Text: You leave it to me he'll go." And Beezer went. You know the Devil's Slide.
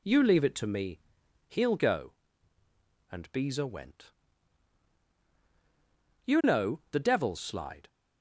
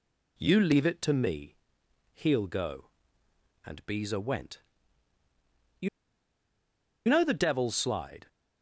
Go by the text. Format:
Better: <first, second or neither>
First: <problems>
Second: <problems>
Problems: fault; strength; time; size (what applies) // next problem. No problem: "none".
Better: first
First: pauses between "me" and "he'll"; noticeable; at 0.9 s; 0.48 s long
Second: pauses between "me" and "he'll"; noticeable; at 1.5 s; 0.58 s long // pauses between "You" and "know"; at 5.8 s; 1.2 s long